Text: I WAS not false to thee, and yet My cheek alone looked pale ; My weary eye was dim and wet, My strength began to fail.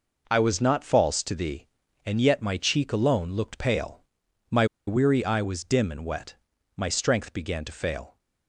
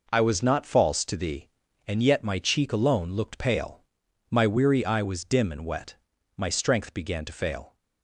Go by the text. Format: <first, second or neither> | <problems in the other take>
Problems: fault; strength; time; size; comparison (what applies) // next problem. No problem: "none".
second | pauses between "My" and "weary"; slight; at 4.6 s; 0.22 s long